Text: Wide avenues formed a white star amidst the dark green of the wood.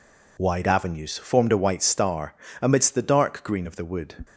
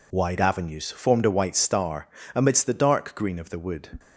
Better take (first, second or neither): neither